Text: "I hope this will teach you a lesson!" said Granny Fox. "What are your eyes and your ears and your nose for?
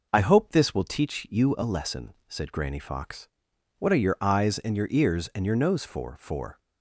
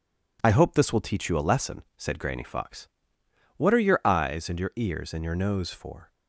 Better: second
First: says "for" twice; at 6.1 s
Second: none

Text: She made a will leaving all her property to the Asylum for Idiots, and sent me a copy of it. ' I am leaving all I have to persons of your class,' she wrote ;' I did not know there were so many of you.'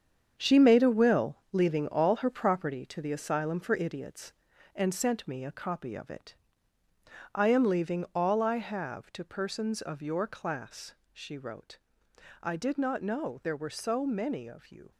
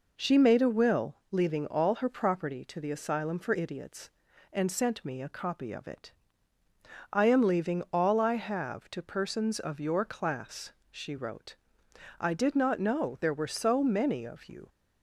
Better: second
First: gets quieter; strong; throughout; 10 dB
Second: none

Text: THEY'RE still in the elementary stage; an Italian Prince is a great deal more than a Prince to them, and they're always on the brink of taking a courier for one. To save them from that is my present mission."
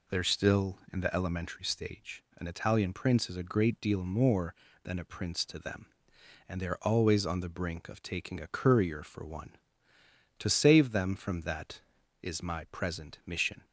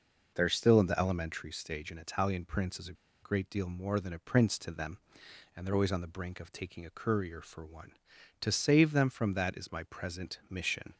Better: first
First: none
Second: pauses between "a" and "great"; slight; at 2.9 s; 0.29 s long

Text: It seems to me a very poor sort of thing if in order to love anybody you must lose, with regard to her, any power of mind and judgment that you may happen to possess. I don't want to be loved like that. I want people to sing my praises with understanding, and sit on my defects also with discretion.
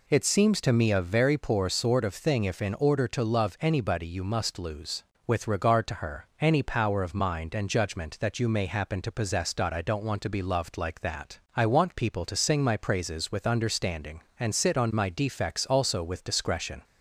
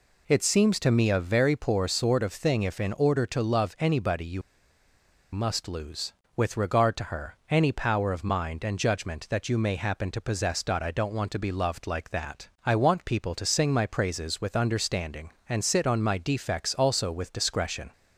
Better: first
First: none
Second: pauses between "you" and "must"; noticeable; at 4.4 s; 0.91 s long

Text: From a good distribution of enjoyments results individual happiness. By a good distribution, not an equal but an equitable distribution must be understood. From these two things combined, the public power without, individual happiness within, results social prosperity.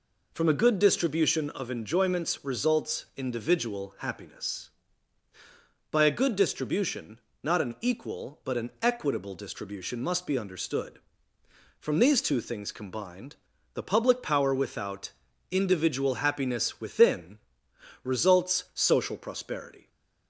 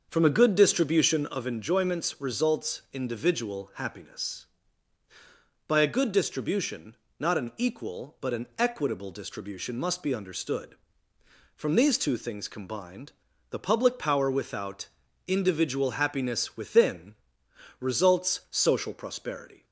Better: first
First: none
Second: starts louder than the rest; until 1.7 s; 6.5 dB

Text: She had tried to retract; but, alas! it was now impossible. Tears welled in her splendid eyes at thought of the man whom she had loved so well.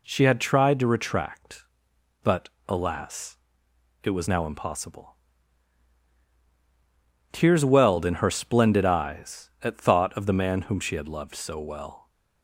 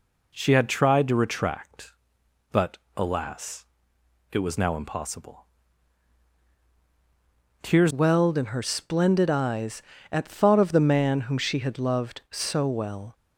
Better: first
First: none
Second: changes voice at "welled"; from 7.9 s on; 5.2 s long

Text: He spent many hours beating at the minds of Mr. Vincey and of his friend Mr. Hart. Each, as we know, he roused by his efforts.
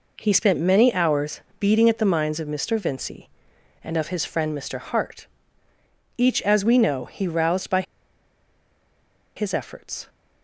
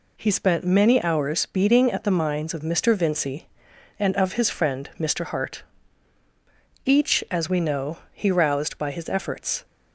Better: second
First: pauses between "hours" and "beating"; slight; at 1.4 s; 0.18 s long // pauses between "by" and "his"; strong; at 7.8 s; 1.5 s long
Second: none

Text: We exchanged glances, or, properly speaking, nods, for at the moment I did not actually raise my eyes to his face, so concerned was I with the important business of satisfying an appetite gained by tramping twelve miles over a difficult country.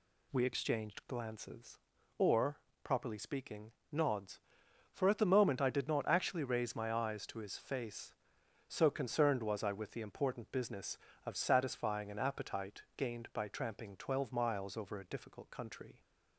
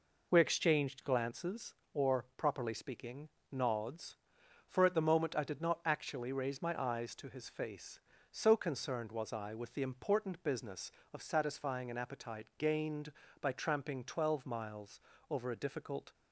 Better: first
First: none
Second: pauses between "miles" and "over"; slight; at 15.0 s; 0.30 s long // stops before "country"; at 16.1 s

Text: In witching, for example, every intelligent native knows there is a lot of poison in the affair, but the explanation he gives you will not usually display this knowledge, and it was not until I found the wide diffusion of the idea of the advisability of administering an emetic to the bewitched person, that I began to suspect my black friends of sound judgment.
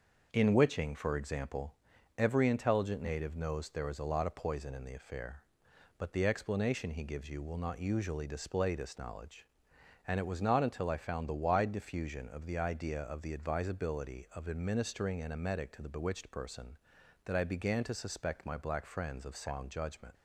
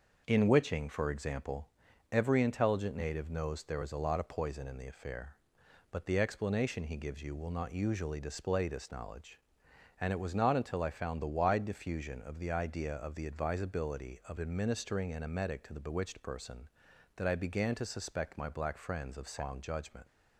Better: neither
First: starts louder than the rest; noticeable; until 1.3 s; 6 dB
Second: starts louder than the rest; noticeable; until 1.2 s; 6 dB

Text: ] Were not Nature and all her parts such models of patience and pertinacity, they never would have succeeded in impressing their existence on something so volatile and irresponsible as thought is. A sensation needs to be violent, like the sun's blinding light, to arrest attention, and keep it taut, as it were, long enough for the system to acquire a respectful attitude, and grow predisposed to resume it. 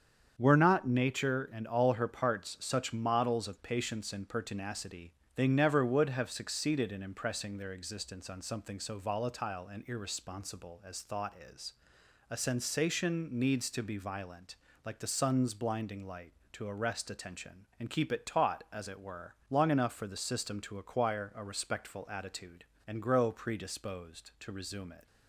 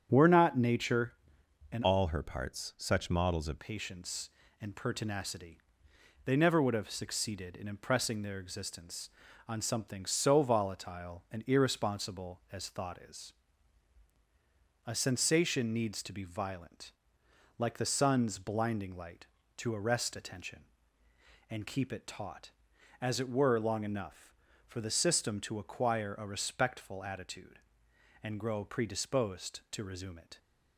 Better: first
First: starts louder than the rest; strong; until 1.4 s; 7.5 dB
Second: starts louder than the rest; strong; until 1.1 s; 8.5 dB // changes voice from "all" to "of"; from 1.8 to 3.5 s; 1.7 s long

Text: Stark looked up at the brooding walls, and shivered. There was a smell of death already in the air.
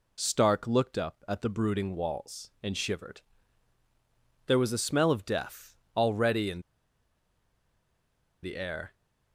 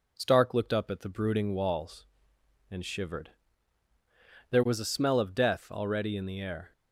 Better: second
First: pauses between "death" and "already"; slight; at 5.7 s; 0.18 s long // pauses between "in" and "the"; strong; at 6.6 s; 1.8 s long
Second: none

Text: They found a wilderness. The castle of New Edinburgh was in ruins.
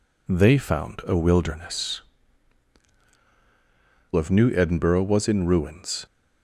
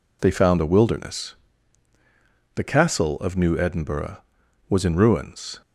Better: second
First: skips "The castle"; at 3.0 s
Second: none

